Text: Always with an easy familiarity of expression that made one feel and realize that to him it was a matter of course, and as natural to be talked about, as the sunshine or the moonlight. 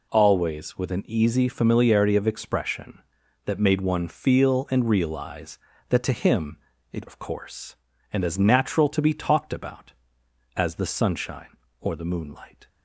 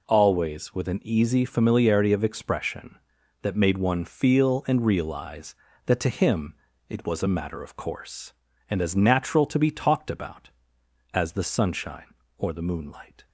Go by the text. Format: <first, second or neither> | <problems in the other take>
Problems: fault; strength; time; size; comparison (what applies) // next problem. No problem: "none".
second | pauses between "him" and "it"; slight; at 6.5 s; 0.34 s long; slight in the second // skips "was a matter"; at 7.0 s